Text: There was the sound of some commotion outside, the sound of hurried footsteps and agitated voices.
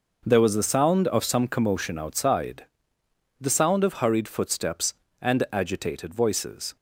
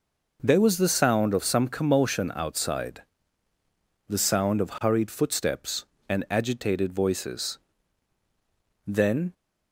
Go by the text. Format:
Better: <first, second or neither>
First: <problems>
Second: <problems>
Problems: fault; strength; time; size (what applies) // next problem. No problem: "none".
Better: first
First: none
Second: goes on to say "Then"; slight; from 8.8 s on; 0.48 s long